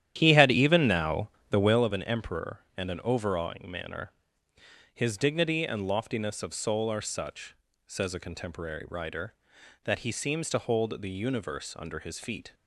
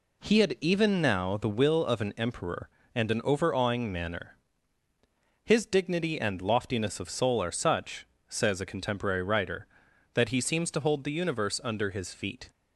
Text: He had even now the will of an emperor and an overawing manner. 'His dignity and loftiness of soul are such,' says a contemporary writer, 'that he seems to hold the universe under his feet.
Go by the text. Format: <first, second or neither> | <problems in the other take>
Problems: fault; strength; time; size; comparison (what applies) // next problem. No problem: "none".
second | starts louder than the rest; strong; until 1.9 s; 11 dB // pauses between "now" and "the"; slight; at 1.2 s; 0.22 s long